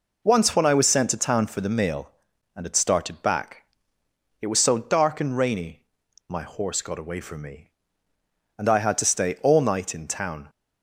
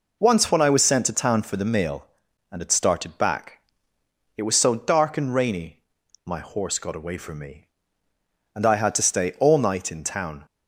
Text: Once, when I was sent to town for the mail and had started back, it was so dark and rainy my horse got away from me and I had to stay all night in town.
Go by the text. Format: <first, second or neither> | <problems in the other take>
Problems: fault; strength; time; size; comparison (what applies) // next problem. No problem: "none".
neither | pauses between "rainy" and "my"; the same in both